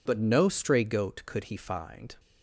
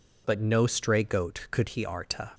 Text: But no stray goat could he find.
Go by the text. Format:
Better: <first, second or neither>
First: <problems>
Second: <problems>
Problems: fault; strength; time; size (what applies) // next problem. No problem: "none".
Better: first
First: none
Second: says "arta" for "find"; at 1.8 s